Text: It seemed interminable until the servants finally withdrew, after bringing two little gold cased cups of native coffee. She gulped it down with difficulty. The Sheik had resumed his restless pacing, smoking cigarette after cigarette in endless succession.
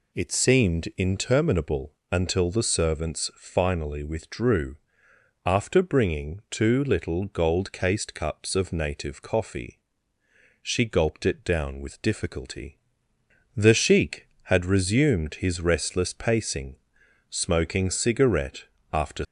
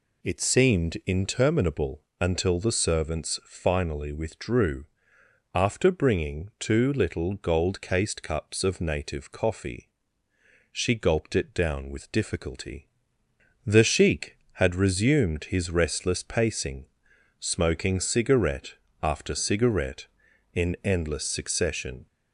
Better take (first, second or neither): second